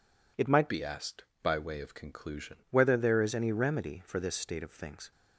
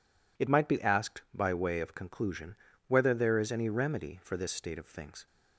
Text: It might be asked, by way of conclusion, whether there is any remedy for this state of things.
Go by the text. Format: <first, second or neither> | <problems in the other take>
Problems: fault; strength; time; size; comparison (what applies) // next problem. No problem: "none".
second | changes voice from "be" to "conclusion"; from 0.6 to 2.5 s; 1.9 s long